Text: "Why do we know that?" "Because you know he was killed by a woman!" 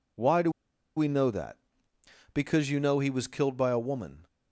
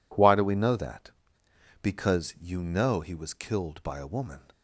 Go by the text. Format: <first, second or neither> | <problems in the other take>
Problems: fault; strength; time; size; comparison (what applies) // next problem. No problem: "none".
second | pauses between "do" and "we"; at 0.5 s; 0.44 s long